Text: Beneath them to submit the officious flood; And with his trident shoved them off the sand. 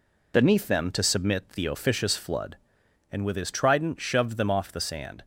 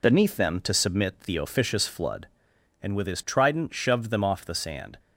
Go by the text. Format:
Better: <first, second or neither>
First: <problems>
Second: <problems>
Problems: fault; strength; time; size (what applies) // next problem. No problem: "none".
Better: neither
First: none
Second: none